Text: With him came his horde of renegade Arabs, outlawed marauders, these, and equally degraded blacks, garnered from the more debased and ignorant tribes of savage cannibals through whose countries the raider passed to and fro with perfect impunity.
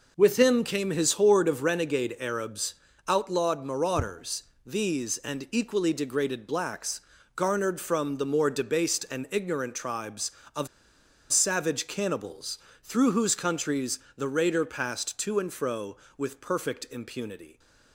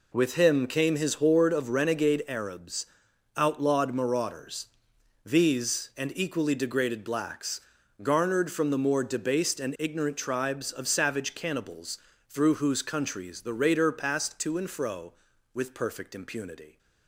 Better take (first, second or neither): second